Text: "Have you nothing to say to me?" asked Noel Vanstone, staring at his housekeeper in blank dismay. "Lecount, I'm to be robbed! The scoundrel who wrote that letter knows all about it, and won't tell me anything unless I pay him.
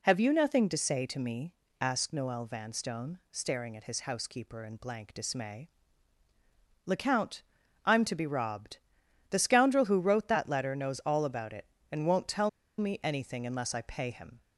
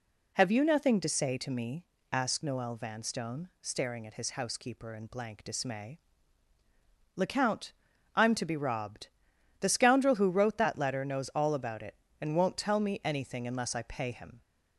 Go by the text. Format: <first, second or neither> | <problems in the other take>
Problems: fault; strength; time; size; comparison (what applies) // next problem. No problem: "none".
second | pauses between "tell" and "me"; slight; at 12.4 s; 0.28 s long